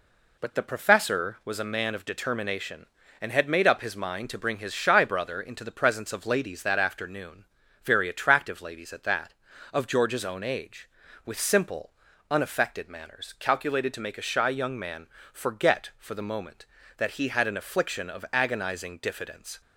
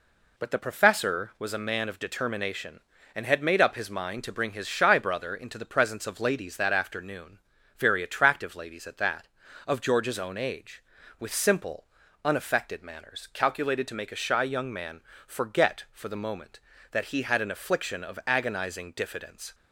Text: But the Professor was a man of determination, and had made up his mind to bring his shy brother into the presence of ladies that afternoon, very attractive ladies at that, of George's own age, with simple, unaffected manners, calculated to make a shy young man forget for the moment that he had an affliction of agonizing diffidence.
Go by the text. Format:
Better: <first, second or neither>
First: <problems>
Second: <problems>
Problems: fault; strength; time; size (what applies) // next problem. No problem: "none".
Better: neither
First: pauses between "man" and "forget"; slight; at 15.0 s; 0.26 s long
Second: pauses between "man" and "forget"; slight; at 15.0 s; 0.26 s long